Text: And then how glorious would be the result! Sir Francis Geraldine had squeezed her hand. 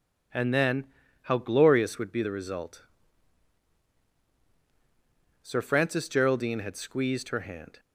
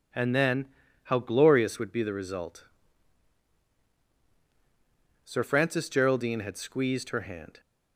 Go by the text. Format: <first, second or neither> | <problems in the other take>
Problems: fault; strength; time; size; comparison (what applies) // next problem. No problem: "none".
neither | pauses between "then" and "how"; the same in both